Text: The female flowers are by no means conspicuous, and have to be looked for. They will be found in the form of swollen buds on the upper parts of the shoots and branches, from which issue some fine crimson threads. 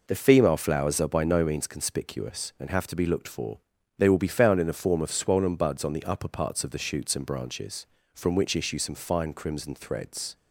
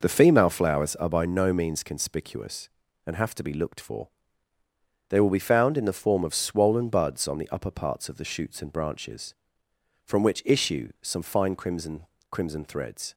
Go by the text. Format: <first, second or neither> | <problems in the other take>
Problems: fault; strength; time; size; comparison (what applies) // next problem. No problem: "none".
first | says "crimson" twice; at 12.3 s